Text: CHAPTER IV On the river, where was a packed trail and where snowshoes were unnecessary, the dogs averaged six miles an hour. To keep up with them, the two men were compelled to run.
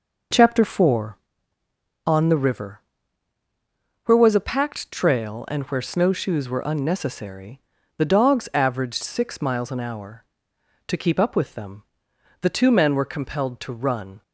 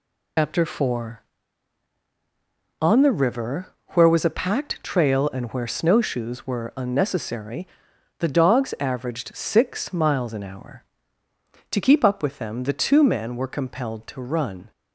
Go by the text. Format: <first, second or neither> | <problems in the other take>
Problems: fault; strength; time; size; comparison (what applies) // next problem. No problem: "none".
first | loses the start of "CHAPTER"; at 0.3 s; 140 ms